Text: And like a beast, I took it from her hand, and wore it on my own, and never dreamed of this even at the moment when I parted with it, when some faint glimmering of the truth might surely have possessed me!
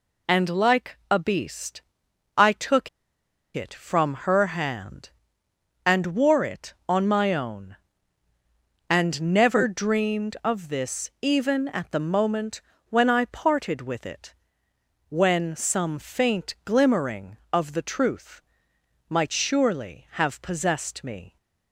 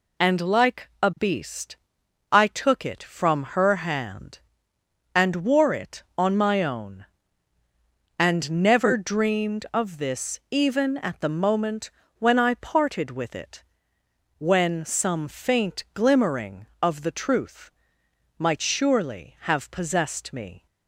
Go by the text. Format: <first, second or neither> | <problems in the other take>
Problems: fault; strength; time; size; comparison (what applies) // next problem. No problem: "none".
second | pauses between "took" and "it"; noticeable; at 2.8 s; 0.65 s long // pauses between "moment" and "when"; slight; at 12.6 s; 0.28 s long; slight in the second // pauses between "truth" and "might"; noticeable; at 18.4 s; 0.68 s long; noticeable in the second